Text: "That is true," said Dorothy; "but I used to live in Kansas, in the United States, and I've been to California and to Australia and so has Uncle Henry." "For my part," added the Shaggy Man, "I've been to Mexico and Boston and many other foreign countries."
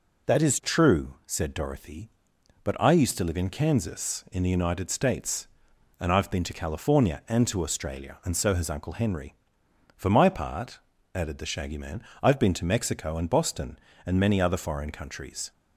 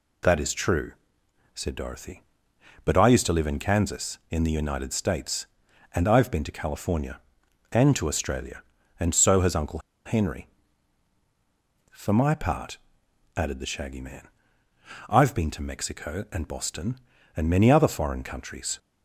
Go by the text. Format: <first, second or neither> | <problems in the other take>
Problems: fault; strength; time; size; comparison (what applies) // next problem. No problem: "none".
first | pauses between "Uncle" and "Henry"; slight; at 9.8 s; 0.25 s long